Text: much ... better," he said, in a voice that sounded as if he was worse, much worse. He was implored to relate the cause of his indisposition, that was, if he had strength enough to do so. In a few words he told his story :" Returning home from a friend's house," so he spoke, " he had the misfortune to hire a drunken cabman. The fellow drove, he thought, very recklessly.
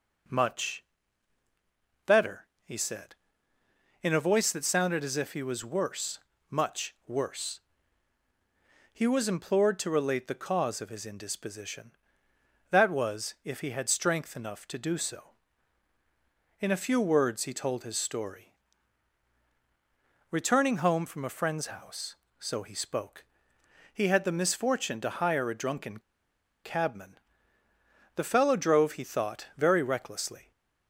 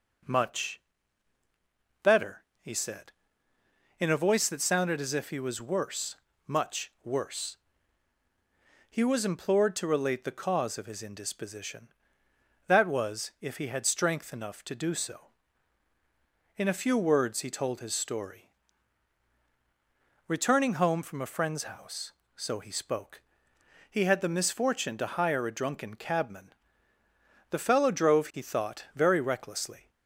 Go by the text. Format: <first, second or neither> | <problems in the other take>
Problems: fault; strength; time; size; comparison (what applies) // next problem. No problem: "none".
second | pauses between "drunken" and "cabman"; noticeable; at 25.9 s; 0.64 s long